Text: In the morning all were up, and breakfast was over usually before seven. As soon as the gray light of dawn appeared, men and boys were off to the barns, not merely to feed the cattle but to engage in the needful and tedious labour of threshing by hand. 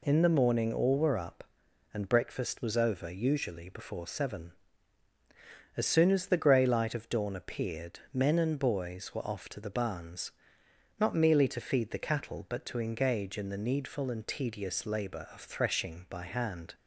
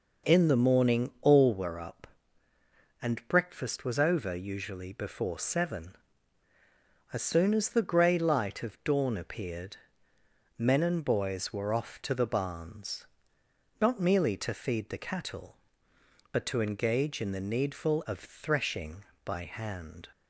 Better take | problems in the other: first | skips "and tedious labour"; at 18.0 s

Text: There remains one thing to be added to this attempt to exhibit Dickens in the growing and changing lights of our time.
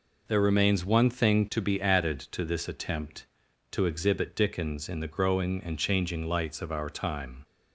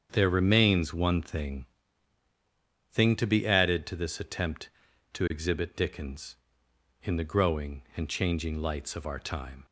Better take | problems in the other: first | starts louder than the rest; strong; until 1.1 s; 7.5 dB // says "thing" twice; at 2.9 s

